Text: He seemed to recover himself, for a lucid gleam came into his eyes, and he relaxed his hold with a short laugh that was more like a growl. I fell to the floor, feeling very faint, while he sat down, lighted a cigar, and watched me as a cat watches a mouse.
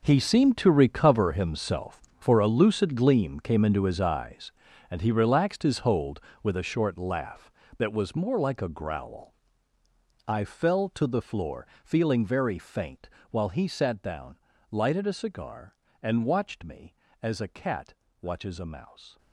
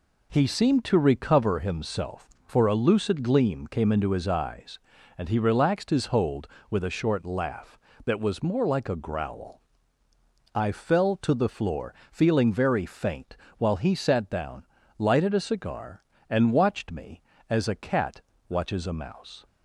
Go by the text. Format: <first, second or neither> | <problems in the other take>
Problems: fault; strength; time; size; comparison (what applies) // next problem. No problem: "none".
second | gets quieter; strong; throughout; 14 dB // pauses between "cat" and "watches"; slight; at 17.9 s; 0.26 s long; slight in the second